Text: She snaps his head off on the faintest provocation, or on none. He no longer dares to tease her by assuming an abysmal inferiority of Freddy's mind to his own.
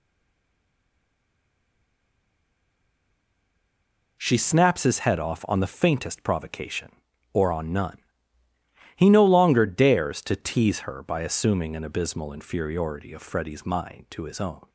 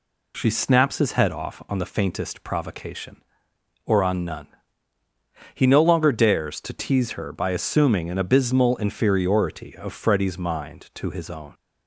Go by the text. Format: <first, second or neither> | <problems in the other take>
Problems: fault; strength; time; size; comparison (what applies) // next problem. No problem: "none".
second | stays silent before the first word; strong; until 4.1 s; 4.1 s long